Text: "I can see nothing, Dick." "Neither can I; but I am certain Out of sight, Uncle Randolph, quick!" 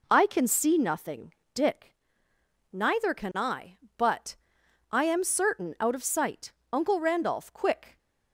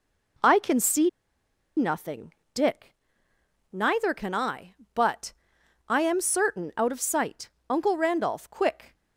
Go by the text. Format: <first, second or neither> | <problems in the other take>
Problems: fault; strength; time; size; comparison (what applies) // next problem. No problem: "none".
first | pauses between "see" and "nothing"; noticeable; at 1.0 s; 0.67 s long // pauses between "but" and "I"; noticeable; at 5.3 s; 0.52 s long; noticeable in the first